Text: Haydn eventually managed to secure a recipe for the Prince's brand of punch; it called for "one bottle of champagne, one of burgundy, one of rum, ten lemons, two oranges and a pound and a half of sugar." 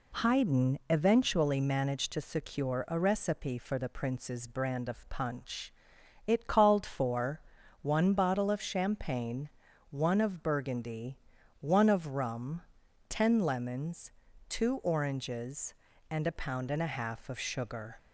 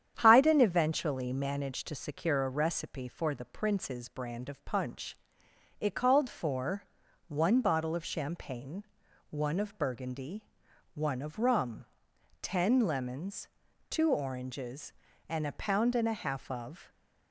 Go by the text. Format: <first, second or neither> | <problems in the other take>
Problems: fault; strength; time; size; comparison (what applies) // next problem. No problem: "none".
first | starts louder than the rest; strong; until 1.2 s; 9 dB // pauses between "for" and "one"; at 6.8 s; 0.42 s long; also in the first // stops before "sugar"; at 16.8 s